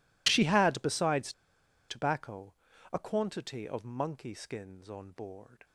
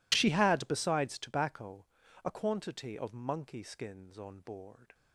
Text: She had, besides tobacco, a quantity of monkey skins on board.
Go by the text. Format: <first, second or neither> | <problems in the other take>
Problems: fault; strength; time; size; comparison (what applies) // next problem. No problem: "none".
second | pauses between "besides" and "tobacco"; noticeable; at 1.3 s; 0.56 s long